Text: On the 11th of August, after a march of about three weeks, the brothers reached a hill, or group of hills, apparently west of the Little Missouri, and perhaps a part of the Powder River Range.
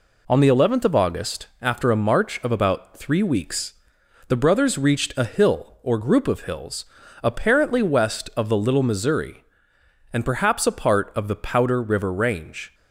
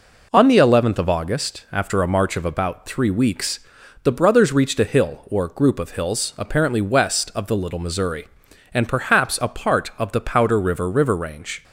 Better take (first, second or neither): first